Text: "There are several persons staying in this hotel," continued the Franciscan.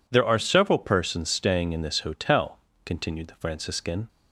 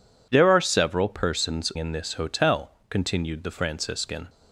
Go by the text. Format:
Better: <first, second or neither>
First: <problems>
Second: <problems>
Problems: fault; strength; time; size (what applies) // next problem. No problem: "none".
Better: first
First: none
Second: skips "staying"; at 1.7 s